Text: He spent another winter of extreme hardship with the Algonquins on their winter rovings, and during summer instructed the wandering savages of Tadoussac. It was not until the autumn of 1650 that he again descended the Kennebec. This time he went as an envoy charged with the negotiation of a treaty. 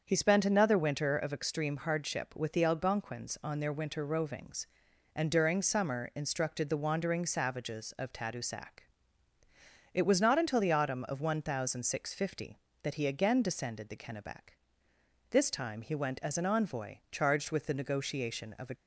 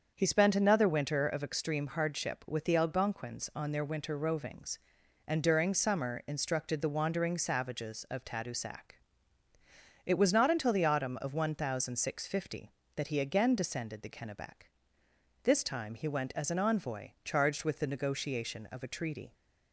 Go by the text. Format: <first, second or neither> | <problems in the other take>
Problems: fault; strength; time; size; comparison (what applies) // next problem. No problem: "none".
second | starts louder than the rest; until 1.0 s; 7 dB; also in the second // stops before "treaty"; at 18.7 s